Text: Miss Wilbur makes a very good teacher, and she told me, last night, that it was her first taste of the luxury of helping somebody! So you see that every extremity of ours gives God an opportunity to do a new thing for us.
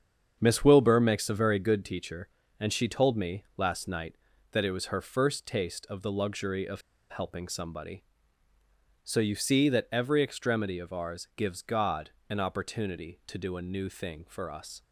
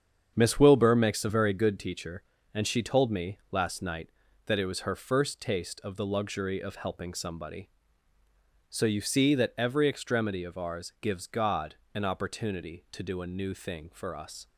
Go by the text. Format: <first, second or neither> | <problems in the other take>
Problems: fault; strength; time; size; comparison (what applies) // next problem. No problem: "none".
second | starts louder than the rest; strong; until 1.4 s; 7.5 dB; strong in the second // pauses between "of" and "helping"; slight; at 6.8 s; 0.29 s long // pauses between "God" and "an"; slight; at 12.1 s; 0.18 s long; slight in the second